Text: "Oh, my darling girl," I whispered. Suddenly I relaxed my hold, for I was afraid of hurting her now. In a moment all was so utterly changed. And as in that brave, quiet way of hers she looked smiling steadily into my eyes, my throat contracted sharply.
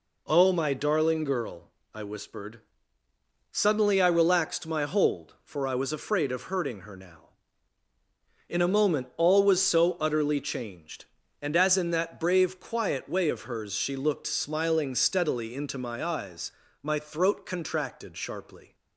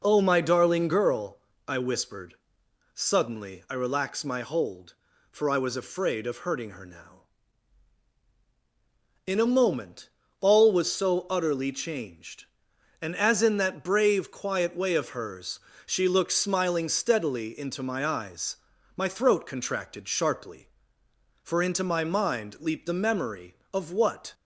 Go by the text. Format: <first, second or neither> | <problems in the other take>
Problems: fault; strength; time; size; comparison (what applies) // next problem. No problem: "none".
first | pauses between "moment" and "all"; slight; at 10.0 s; 0.30 s long // pauses between "hers" and "she"; slight; at 15.5 s; 0.26 s long // goes on to say "For into my mind leaped the memory of what"; strong; from 21.4 s on; 2.9 s long